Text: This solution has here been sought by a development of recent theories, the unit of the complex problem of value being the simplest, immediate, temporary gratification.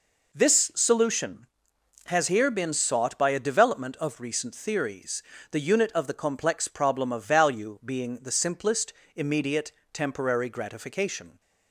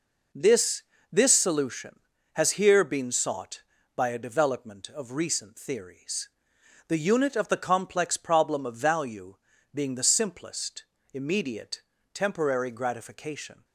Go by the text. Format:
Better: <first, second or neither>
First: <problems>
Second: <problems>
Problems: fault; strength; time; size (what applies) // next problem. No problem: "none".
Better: first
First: none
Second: says "This" twice; at 1.1 s // pauses between "value" and "being"; at 9.3 s; 0.40 s long